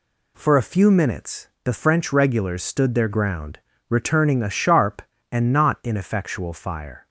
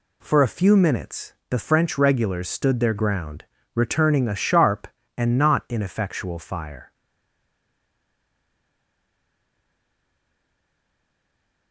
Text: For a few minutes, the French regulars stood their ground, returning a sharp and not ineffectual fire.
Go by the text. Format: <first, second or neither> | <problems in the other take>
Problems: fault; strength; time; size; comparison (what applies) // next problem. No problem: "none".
first | stays silent after the last word; strong; from 6.9 s on; 4.8 s long